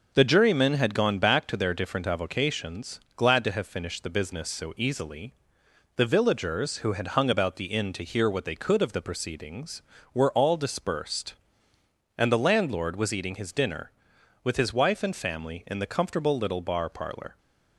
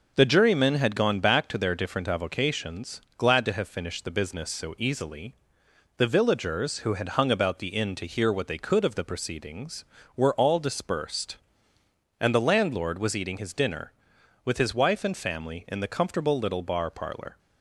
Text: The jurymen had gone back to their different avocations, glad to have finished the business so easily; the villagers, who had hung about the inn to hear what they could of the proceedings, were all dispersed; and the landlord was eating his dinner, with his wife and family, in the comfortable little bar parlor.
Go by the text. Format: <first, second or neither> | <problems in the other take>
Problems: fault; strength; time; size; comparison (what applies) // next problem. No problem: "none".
neither | none